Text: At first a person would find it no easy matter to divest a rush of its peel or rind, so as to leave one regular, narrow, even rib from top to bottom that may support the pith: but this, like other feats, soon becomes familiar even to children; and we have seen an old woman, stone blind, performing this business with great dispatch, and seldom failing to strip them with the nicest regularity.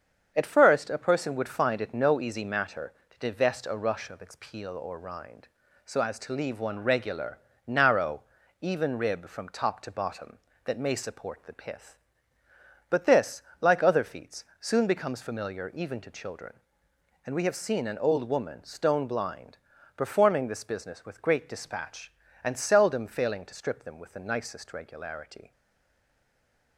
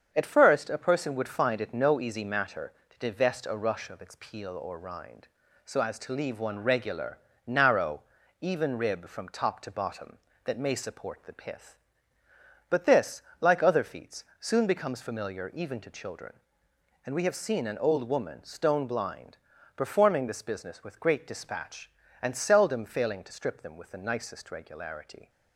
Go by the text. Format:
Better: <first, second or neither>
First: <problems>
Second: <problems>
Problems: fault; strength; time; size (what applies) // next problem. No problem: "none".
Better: second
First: starts louder than the rest; strong; until 1.3 s; 7.5 dB // stays silent after the last word; noticeable; from 25.5 s on; 1.2 s long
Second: starts louder than the rest; strong; until 1.1 s; 7.5 dB